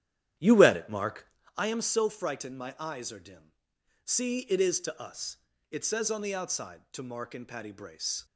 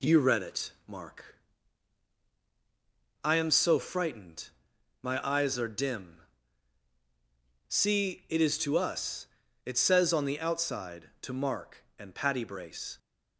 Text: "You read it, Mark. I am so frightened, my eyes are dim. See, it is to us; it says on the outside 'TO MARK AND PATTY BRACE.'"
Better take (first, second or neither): second